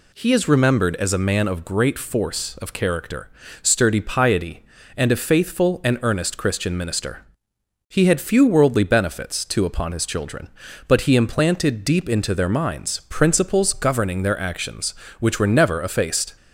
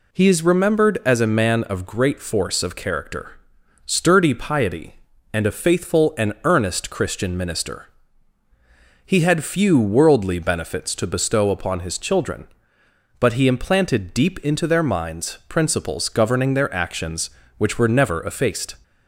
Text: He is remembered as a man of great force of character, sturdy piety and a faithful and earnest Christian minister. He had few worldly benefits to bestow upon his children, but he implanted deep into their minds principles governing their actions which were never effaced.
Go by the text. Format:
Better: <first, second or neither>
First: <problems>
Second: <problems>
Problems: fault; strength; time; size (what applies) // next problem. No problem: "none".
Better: second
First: skips "bestow"; at 9.6 s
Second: none